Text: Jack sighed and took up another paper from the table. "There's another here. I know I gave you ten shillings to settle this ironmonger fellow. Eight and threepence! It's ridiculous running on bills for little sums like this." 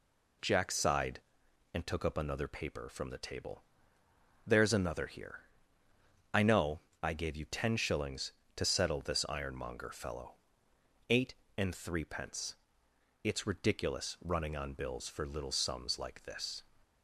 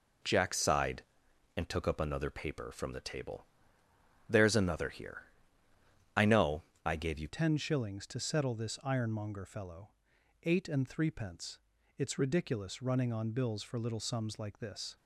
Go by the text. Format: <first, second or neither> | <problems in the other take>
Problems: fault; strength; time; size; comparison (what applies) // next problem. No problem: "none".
first | pauses between "know" and "I"; slight; at 6.6 s; 0.20 s long; slight in the first // changes voice at "ten"; from 7.2 s on; 7.7 s long